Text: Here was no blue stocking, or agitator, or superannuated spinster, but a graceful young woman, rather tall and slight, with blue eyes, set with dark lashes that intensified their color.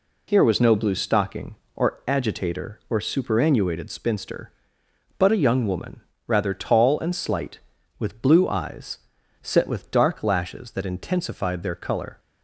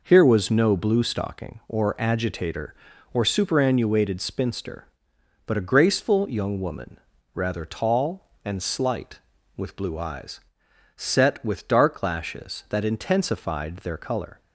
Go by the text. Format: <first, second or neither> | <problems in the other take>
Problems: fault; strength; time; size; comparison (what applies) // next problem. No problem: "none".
second | skips "graceful"; at 5.4 s